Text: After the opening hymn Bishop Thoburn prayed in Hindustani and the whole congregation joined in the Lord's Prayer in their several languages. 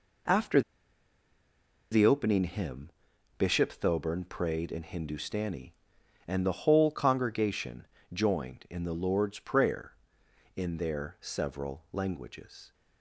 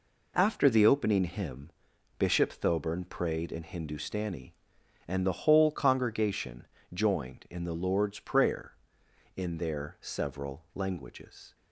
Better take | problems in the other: second | pauses between "After" and "the"; strong; at 0.6 s; 1.3 s long // pauses between "hymn" and "Bishop"; noticeable; at 2.8 s; 0.50 s long; noticeable in the second // pauses between "congregation" and "joined"; slight; at 7.8 s; 0.26 s long; slight in the second

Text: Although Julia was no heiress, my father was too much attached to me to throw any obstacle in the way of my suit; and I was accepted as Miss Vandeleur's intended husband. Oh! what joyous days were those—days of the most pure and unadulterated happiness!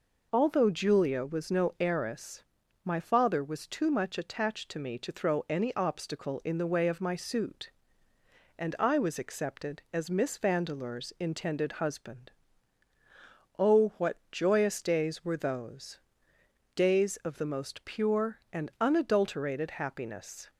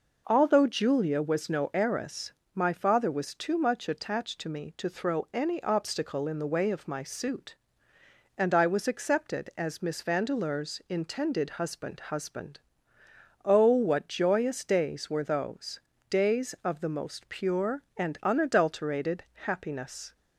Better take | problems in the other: first | says "husband" twice; at 12.0 s // pauses between "unadulterated" and "happiness"; slight; at 19.2 s; 0.18 s long

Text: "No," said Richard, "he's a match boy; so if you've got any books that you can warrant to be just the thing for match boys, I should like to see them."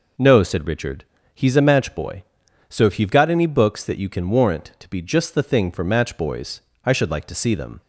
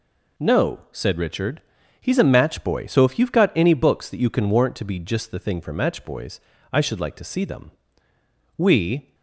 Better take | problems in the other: first | goes on to say "We"; from 8.5 s on; 0.56 s long

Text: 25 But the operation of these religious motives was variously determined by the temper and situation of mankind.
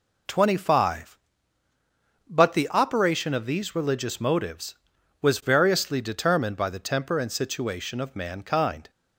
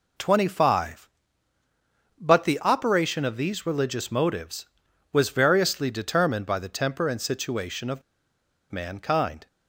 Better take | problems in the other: first | pauses between "of" and "mankind"; noticeable; at 8.0 s; 0.70 s long

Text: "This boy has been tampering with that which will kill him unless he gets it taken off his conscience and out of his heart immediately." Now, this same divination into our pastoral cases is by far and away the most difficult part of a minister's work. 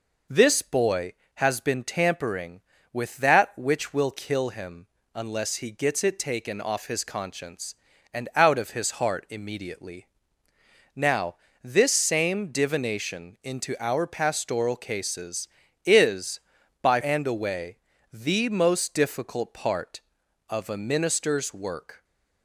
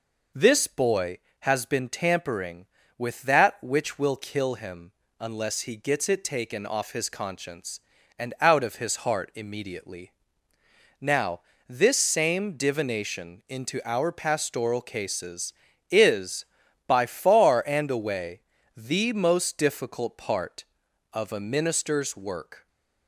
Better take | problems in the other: second | pauses between "him" and "unless"; slight; at 4.8 s; 0.28 s long; slight in the second // skips "far"; at 17.0 s // pauses between "away" and "the"; slight; at 17.7 s; 0.34 s long; slight in the second

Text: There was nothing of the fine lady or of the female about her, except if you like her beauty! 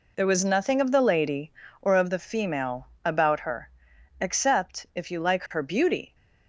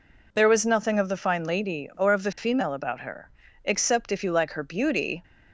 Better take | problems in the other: second | skips "fine"; at 0.9 s // pauses between "female" and "about"; slight; at 2.8 s; 0.16 s long

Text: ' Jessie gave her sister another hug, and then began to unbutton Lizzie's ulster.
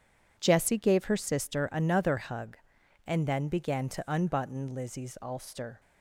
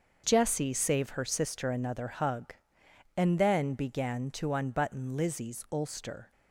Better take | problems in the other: first | starts louder than the rest; until 1.2 s; 6.5 dB // says "save" for "gave"; at 0.7 s

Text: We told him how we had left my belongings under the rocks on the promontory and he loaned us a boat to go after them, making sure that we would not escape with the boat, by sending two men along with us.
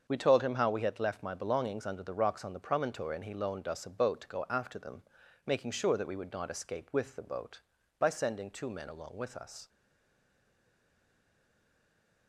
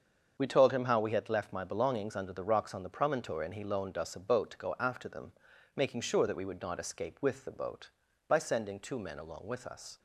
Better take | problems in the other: second | starts louder than the rest; until 1.1 s; 7 dB; also in the second // stays silent after the last word; strong; from 9.6 s on; 2.6 s long

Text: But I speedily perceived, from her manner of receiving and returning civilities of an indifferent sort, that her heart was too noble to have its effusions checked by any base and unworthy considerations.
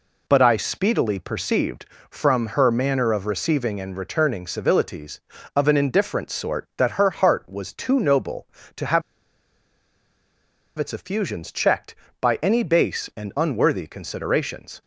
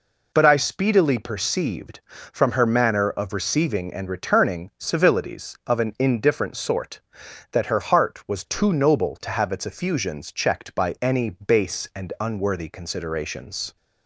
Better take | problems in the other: second | pauses between "have" and "its"; strong; at 9.0 s; 1.7 s long

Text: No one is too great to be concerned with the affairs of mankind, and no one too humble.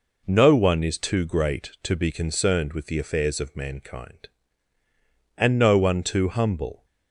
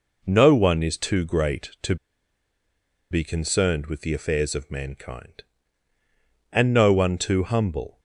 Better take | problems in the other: first | pauses between "to" and "be"; at 1.9 s; 1.1 s long

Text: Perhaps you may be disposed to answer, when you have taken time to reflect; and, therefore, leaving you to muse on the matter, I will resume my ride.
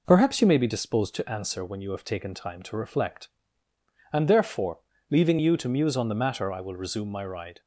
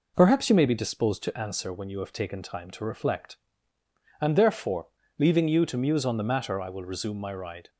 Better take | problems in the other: neither | none

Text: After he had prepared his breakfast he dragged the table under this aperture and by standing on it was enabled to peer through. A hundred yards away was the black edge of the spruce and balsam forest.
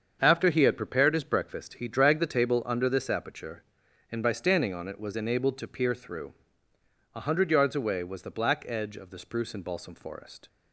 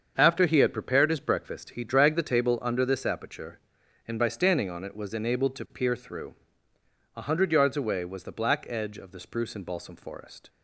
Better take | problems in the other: neither | starts louder than the rest; the same in both

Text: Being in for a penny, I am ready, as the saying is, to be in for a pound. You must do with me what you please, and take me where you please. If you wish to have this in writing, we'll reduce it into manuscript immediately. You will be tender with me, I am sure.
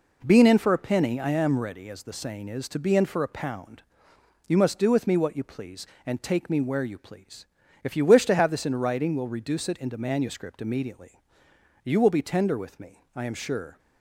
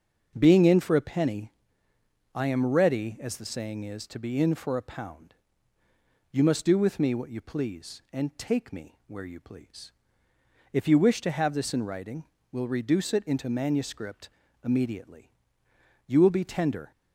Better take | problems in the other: first | starts louder than the rest; until 1.3 s; 6.5 dB // pauses between "manuscript" and "immediately"; slight; at 14.2 s; 0.34 s long // stops before "with me I am sure"; at 16.9 s

